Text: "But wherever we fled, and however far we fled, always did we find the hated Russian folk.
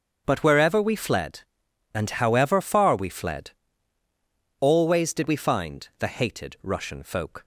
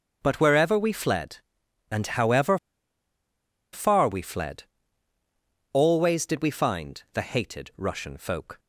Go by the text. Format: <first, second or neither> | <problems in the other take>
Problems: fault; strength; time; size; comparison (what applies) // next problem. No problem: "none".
first | starts louder than the rest; until 1.2 s; 7 dB; also in the first // pauses between "however" and "far"; at 2.5 s; 1.1 s long